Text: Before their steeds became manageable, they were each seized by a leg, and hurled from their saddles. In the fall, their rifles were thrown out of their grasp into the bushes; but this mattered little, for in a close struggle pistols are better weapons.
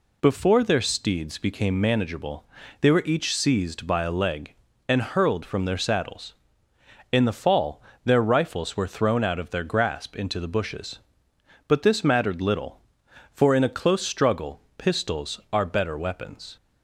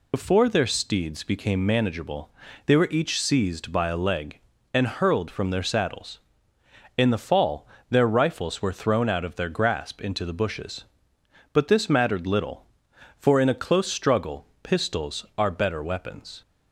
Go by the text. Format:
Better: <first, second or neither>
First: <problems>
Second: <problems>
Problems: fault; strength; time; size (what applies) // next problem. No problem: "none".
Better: first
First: pauses between "struggle" and "pistols"; slight; at 14.6 s; 0.16 s long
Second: loses the start of "Before"; at 0.1 s; 65 ms // pauses between "struggle" and "pistols"; slight; at 14.4 s; 0.16 s long